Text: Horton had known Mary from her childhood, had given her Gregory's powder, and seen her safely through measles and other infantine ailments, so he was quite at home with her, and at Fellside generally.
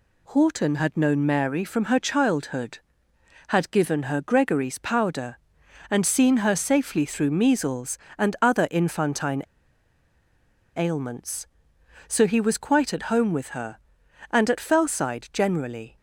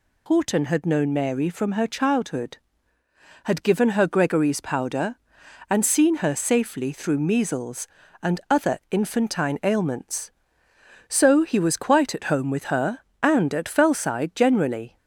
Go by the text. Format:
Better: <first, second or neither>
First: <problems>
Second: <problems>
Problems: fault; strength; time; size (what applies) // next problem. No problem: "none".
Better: second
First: pauses between "infantine" and "ailments"; strong; at 9.4 s; 1.3 s long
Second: none